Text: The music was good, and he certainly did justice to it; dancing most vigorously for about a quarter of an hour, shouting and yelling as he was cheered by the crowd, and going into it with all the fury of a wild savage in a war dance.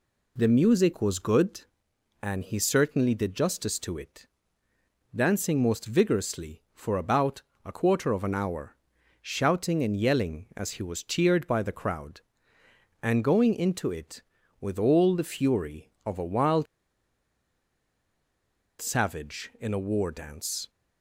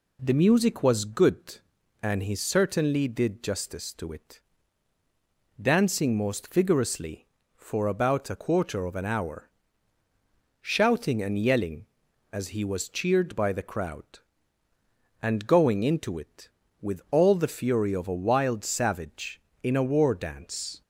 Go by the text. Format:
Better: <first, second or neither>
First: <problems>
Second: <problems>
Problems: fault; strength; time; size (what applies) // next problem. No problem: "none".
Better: second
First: pauses between "about" and "a"; slight; at 7.4 s; 0.24 s long // pauses between "wild" and "savage"; strong; at 16.6 s; 2.1 s long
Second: none